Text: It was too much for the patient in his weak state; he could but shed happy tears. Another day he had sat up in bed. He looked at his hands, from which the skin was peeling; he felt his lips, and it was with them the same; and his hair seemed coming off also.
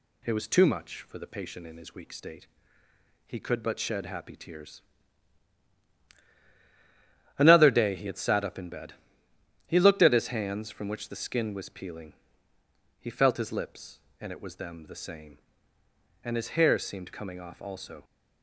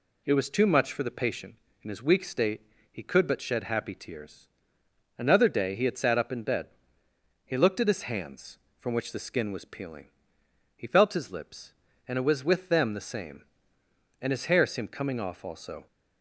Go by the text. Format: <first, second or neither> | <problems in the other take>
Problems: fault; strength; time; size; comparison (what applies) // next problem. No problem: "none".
second | skips "with"; at 14.5 s